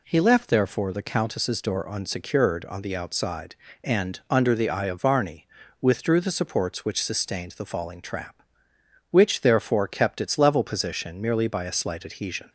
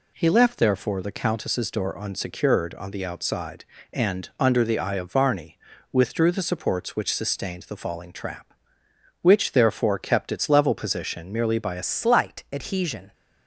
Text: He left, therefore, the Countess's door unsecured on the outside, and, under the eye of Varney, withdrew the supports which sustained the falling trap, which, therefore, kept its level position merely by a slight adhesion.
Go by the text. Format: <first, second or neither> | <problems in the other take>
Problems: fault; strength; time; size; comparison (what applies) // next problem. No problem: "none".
first | changes voice at "slight"; from 11.8 s on; 1.3 s long